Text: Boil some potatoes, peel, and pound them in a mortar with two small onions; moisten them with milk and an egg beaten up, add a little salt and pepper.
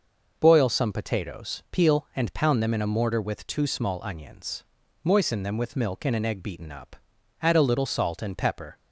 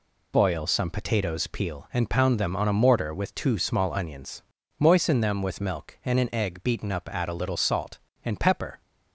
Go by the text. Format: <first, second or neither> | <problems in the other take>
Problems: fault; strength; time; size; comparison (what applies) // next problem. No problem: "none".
first | says "on" for "in"; at 2.5 s